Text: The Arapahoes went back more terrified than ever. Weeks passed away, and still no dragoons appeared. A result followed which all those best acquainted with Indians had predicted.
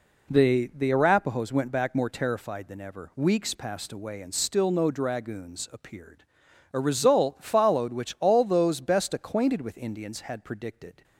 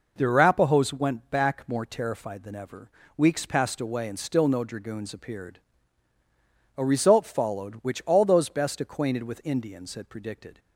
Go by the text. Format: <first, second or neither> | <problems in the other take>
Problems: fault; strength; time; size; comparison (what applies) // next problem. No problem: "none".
second | says "The" twice; at 0.7 s